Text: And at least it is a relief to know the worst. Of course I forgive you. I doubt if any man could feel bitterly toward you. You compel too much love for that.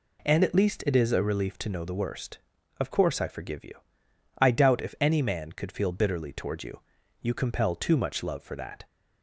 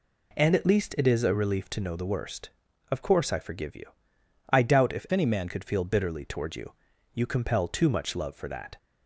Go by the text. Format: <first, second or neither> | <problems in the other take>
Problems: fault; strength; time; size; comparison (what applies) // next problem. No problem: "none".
first | changes voice from "any" to "man"; from 5.1 to 5.4 s; 0.3 s long